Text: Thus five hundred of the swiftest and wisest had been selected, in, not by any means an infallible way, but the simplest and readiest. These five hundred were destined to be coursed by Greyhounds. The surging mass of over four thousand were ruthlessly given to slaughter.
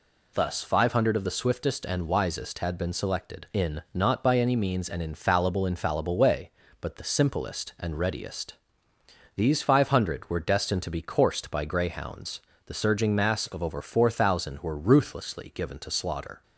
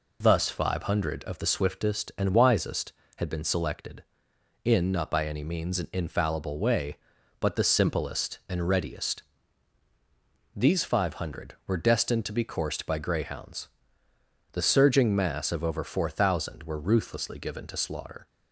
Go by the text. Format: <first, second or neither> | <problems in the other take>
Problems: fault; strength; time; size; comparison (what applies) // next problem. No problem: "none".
second | says "infallible" twice; at 5.6 s